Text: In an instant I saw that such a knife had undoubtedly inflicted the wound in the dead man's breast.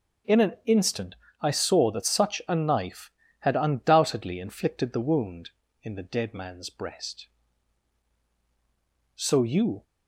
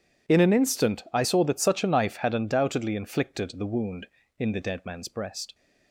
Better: second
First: pauses between "instant" and "I"; slight; at 1.1 s; 0.26 s long // goes on to say "So you"; noticeable; from 9.1 s on; 0.68 s long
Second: none

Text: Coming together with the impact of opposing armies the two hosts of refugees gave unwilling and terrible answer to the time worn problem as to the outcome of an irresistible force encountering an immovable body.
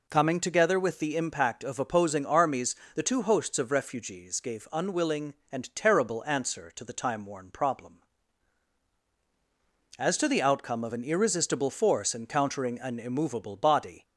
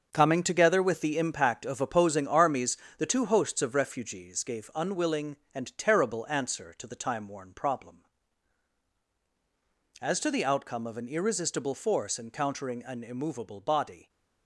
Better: first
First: pauses between "armies" and "the"; slight; at 2.7 s; 0.19 s long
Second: gets quieter; strong; throughout; 9 dB // pauses between "armies" and "the"; slight; at 2.7 s; 0.20 s long

